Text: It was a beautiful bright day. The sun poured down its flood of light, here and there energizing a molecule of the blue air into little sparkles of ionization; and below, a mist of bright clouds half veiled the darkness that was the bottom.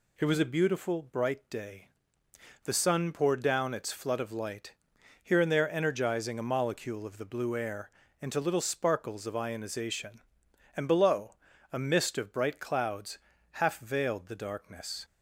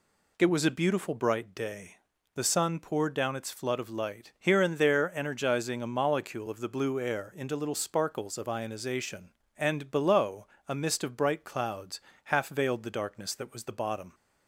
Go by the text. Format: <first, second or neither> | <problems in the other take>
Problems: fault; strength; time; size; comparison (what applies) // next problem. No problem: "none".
second | pauses between "air" and "into"; slight; at 7.9 s; 0.28 s long // pauses between "clouds" and "half"; slight; at 13.1 s; 0.32 s long; slight in the second // stops before "that was the bottom"; at 15.0 s